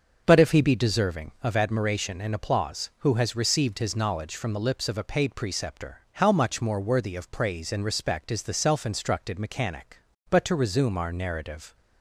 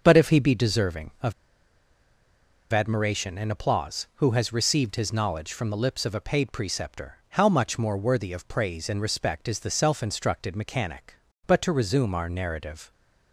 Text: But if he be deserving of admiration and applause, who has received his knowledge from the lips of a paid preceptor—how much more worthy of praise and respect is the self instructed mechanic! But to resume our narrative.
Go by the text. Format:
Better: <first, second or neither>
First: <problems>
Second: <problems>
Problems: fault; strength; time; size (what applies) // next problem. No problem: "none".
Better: first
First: starts louder than the rest; until 1.2 s; 6.5 dB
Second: starts louder than the rest; until 1.0 s; 6.5 dB // pauses between "of" and "admiration"; strong; at 1.3 s; 1.4 s long